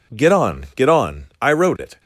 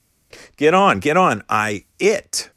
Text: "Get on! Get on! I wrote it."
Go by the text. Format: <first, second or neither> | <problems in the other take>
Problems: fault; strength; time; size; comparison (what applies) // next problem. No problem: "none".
first | skips "wrote"; at 1.9 s